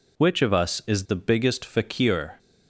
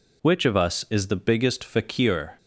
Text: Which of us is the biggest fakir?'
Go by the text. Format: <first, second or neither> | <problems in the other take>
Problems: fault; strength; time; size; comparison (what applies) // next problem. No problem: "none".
neither | none